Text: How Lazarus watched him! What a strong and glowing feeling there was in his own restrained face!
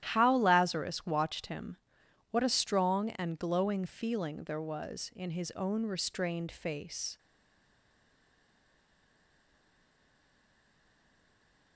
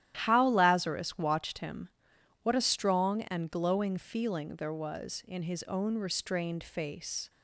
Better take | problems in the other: second | starts louder than the rest; strong; until 1.0 s; 12 dB; strong in the second // stays silent after the last word; strong; from 7.1 s on; 4.6 s long

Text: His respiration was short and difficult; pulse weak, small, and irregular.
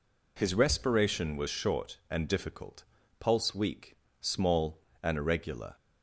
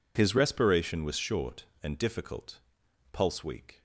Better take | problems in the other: first | stops before "small and irregular"; at 3.7 s

